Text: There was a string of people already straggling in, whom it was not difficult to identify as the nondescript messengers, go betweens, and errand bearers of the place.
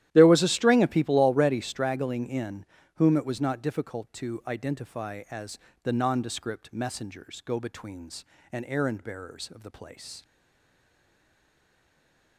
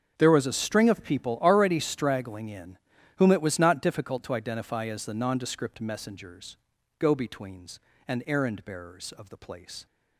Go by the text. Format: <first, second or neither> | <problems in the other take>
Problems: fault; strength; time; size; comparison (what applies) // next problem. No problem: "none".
second | starts louder than the rest; strong; until 1.1 s; 12.5 dB; also in the second // pauses between "as" and "the"; slight; at 5.5 s; 0.24 s long // stays silent after the last word; from 10.2 s on; 2.1 s long